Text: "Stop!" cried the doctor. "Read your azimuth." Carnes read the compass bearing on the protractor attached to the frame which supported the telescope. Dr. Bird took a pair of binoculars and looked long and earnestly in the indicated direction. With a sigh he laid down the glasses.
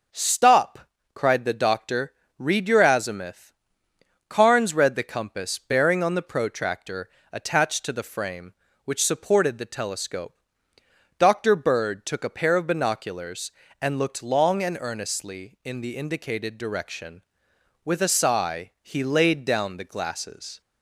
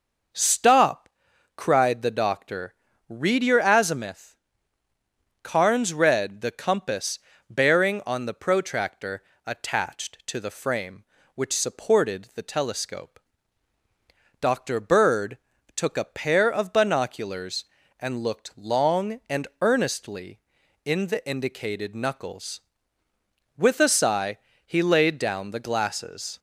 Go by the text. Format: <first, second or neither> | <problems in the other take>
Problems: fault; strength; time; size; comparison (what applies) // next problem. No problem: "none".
first | pauses between "compass" and "bearing"; slight; at 7.1 s; 0.32 s long // pauses between "protractor" and "attached"; slight; at 9.2 s; 0.22 s long; slight in the first // pauses between "Bird" and "took"; at 15.3 s; 0.38 s long // says "knuckles" for "direction"; at 21.9 s // pauses between "sigh" and "he"; slight; at 24.3 s; 0.26 s long